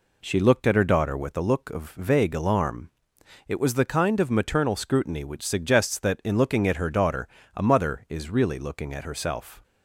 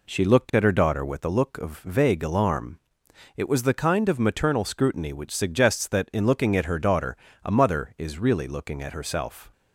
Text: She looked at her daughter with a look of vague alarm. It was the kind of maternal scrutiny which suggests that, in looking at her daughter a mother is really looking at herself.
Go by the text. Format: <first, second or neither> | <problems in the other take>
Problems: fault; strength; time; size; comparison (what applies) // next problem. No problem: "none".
neither | pauses between "daughter" and "a"; slight; the same in both